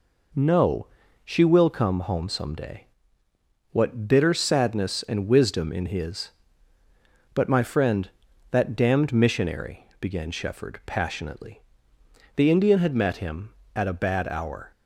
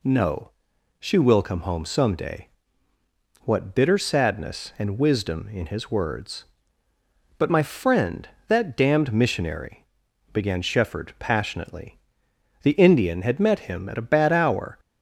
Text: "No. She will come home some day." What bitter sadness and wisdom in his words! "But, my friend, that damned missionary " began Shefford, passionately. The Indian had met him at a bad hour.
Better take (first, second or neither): second